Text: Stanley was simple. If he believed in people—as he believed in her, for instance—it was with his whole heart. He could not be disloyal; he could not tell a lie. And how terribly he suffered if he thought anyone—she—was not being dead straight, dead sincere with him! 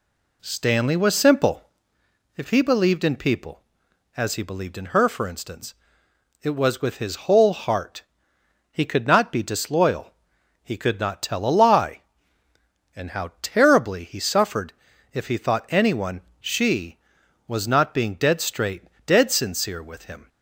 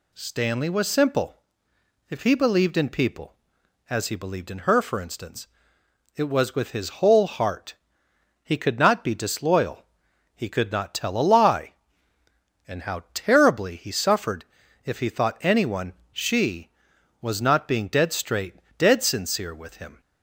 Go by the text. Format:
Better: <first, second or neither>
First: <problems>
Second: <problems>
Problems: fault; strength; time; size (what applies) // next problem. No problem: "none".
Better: second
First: starts louder than the rest; slight; until 2.1 s; 2 dB // pauses between "suffered" and "if"; at 14.7 s; 0.40 s long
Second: pauses between "suffered" and "if"; at 14.4 s; 0.40 s long